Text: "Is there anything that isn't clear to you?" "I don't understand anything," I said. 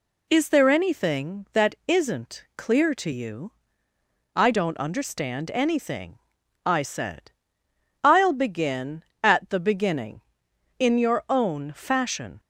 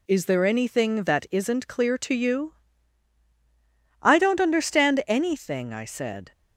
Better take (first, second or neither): second